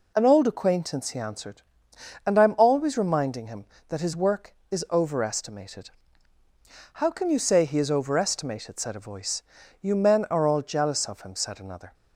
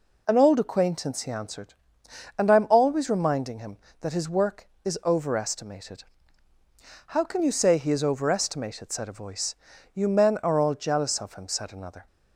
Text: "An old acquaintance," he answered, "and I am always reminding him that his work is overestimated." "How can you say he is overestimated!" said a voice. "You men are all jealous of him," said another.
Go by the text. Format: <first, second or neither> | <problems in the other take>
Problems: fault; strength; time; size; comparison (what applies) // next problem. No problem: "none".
neither | none